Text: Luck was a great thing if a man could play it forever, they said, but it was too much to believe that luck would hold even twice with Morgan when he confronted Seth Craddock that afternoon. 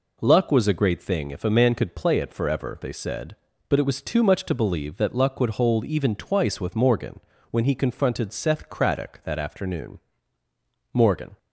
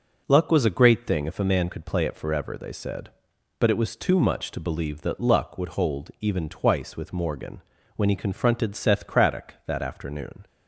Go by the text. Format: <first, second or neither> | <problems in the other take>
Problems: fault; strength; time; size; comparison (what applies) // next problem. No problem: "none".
second | pauses between "Morgan" and "when"; slight; at 7.1 s; 0.32 s long; slight in the second // goes on to say "Morgan"; slight; from 10.9 s on; 0.46 s long